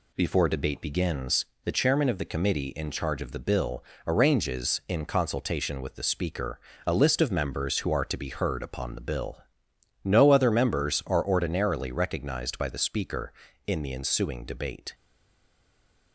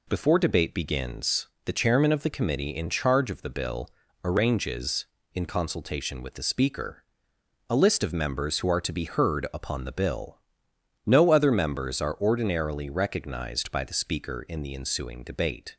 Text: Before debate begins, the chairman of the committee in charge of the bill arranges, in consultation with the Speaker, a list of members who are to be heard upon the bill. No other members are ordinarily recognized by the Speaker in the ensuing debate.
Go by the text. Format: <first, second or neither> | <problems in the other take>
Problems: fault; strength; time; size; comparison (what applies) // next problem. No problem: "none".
second | pauses between "bill" and "arranges"; slight; at 3.8 s; 0.24 s long; slight in the second // stays silent after the last word; noticeable; from 14.9 s on; 1.2 s long